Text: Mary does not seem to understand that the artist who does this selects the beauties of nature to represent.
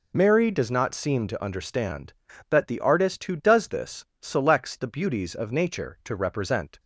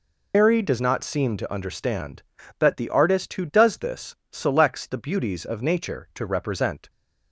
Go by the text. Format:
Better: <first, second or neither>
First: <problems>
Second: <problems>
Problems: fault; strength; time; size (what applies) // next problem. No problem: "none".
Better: first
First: pauses between "this" and "selects"; slight; at 4.0 s; 0.16 s long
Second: loses the start of "Mary"; at 0.3 s; 95 ms // pauses between "this" and "selects"; slight; at 4.1 s; 0.16 s long